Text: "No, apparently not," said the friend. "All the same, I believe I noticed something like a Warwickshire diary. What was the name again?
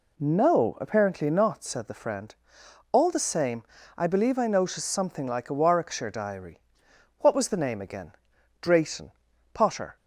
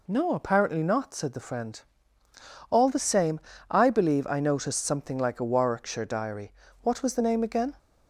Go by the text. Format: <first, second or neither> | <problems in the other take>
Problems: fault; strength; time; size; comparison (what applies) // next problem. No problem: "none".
second | goes on to say "Drayton Potter"; from 8.6 s on; 1.3 s long